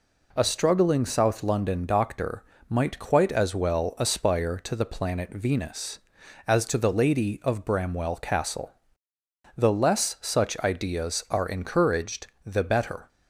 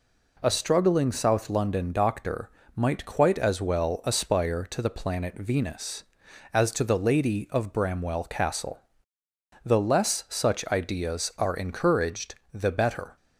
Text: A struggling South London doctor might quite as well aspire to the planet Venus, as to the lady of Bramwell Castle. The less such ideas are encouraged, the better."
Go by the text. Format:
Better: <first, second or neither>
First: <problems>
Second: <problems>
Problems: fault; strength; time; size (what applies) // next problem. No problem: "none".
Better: neither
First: pauses between "doctor" and "might"; slight; at 2.4 s; 0.26 s long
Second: pauses between "doctor" and "might"; slight; at 2.4 s; 0.26 s long